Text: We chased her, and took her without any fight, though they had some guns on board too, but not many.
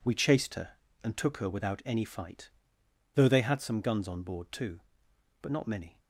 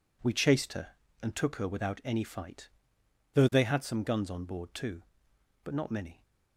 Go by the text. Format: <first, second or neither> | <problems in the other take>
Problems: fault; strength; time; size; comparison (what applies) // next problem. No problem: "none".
neither | none